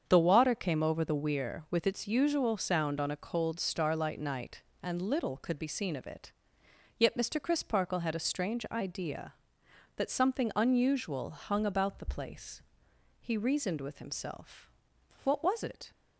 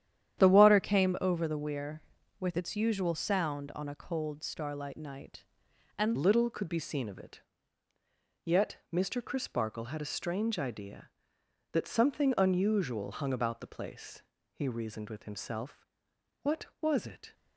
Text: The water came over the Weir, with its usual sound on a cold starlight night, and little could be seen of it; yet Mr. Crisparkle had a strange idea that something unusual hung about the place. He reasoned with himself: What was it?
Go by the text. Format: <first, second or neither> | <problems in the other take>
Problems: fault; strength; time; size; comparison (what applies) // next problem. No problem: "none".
first | starts louder than the rest; strong; until 1.4 s; 10 dB; strong in the first // changes voice at "little"; from 6.1 s on; 11.2 s long